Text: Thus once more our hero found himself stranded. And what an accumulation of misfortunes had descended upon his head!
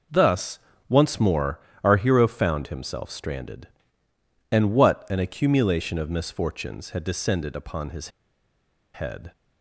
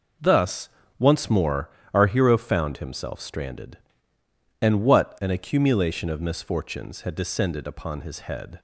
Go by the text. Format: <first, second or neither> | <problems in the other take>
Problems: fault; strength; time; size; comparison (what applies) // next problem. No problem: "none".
second | pauses between "Thus" and "once"; slight; at 0.5 s; 0.30 s long; slight in the second // pauses between "more" and "our"; slight; at 1.5 s; 0.24 s long; slight in the second // pauses between "his" and "head"; noticeable; at 8.0 s; 0.85 s long